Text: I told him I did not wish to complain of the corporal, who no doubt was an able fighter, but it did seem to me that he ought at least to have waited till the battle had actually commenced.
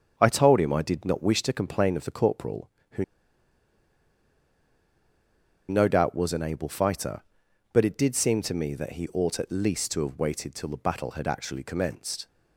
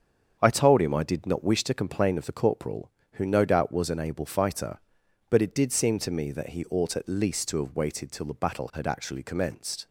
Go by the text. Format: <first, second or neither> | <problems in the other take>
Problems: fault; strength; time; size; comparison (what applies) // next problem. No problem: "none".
second | starts louder than the rest; strong; until 1.1 s; 7.5 dB; strong in the second // pauses between "who" and "no"; strong; at 3.0 s; 2.6 s long